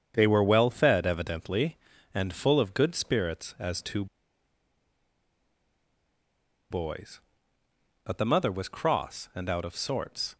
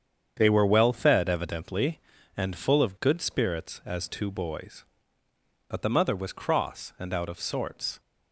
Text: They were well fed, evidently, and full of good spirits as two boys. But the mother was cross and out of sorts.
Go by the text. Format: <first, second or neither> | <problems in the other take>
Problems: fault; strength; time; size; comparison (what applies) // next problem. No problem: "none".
second | starts louder than the rest; strong; until 1.1 s; 7.5 dB; strong in the second // pauses between "two" and "boys"; strong; at 4.0 s; 2.6 s long